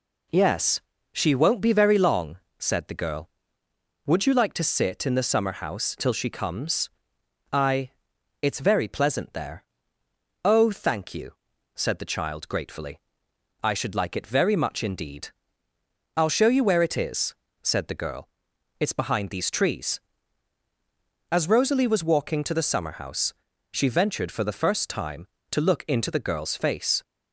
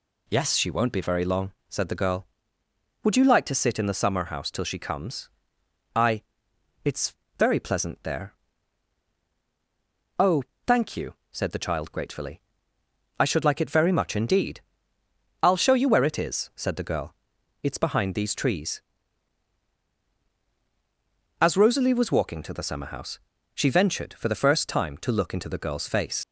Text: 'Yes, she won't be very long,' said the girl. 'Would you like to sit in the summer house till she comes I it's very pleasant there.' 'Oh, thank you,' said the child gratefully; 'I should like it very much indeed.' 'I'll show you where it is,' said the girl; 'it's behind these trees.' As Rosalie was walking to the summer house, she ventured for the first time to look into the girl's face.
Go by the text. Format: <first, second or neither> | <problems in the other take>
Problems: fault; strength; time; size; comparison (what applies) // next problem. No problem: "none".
first | pauses between "comes" and "I"; noticeable; at 5.2 s; 0.66 s long; noticeable in the first // pauses between "I" and "it's"; noticeable; at 6.2 s; 0.62 s long; noticeable in the first // pauses between "it's" and "very"; slight; at 7.1 s; 0.24 s long // leaves "face" unfinished; at 26.2 s; 70 ms